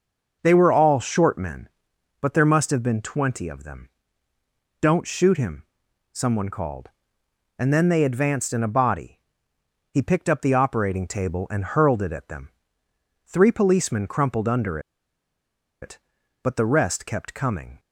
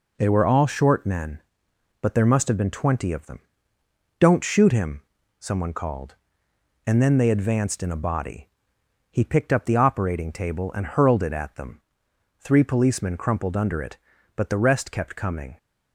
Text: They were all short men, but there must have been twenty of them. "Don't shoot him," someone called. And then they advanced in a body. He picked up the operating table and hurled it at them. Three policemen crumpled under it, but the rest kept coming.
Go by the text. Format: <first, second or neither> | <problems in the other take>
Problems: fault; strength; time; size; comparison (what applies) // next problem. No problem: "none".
second | starts louder than the rest; until 1.4 s; 6 dB // pauses between "under" and "it"; at 14.7 s; 1.0 s long